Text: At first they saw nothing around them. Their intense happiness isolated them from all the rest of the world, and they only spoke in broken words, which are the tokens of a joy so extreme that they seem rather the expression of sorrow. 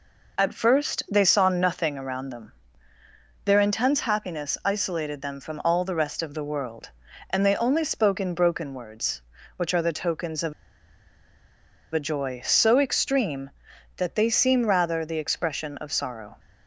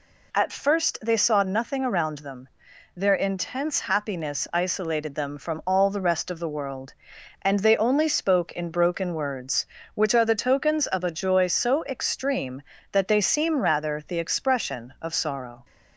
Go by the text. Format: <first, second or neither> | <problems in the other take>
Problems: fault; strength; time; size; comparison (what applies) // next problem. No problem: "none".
second | pauses between "of" and "a"; strong; at 10.5 s; 1.4 s long